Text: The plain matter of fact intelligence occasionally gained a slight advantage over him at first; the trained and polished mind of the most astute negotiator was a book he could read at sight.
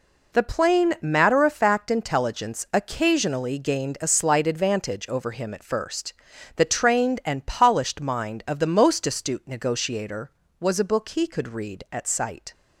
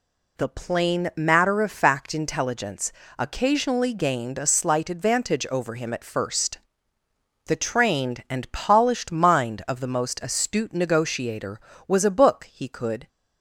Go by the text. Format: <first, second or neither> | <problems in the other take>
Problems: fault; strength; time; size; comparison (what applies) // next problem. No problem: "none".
first | pauses between "intelligence" and "occasionally"; slight; at 2.9 s; 0.26 s long // stops before "read at sight"; at 13.0 s